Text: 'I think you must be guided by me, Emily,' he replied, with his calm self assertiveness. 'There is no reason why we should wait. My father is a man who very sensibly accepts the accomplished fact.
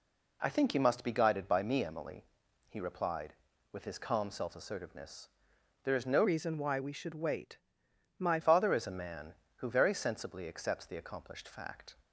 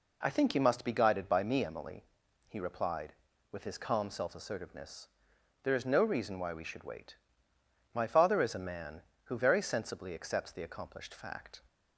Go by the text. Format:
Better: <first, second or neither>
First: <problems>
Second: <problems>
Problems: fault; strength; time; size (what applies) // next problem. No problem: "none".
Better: second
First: changes voice from "reason" to "My"; from 6.2 to 8.3 s; 2.1 s long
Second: none